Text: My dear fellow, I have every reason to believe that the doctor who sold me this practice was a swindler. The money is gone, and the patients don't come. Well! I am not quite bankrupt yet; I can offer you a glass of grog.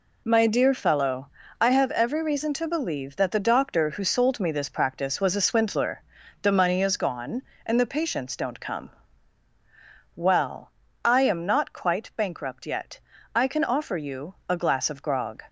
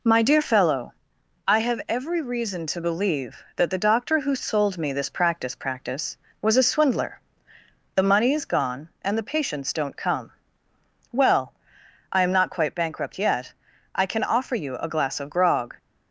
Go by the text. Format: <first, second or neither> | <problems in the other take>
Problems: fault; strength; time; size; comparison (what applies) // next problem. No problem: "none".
first | says "practice" twice; at 5.5 s